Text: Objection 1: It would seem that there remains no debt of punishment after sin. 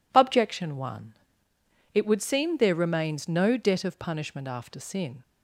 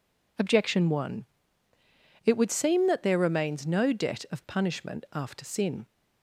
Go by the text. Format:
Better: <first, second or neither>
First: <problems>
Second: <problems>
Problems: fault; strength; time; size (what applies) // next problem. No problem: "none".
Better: second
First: skips "that"; at 2.5 s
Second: none